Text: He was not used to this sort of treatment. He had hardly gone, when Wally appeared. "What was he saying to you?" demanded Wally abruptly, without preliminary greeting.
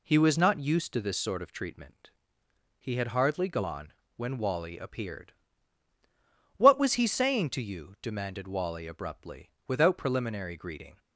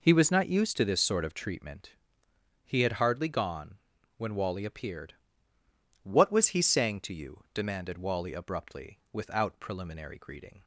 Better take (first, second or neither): neither